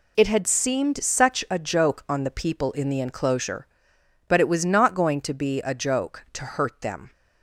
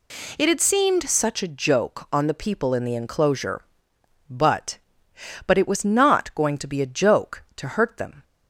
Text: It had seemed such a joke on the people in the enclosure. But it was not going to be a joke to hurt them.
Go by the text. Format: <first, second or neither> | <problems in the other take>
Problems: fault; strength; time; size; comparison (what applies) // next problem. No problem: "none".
first | says "But" twice; at 5.4 s